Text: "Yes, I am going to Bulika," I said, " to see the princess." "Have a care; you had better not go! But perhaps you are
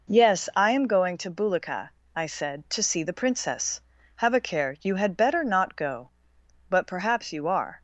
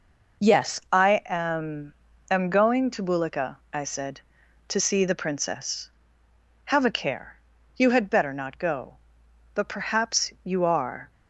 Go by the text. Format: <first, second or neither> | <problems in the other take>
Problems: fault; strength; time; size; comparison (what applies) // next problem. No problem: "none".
first | says "am" twice; at 2.2 s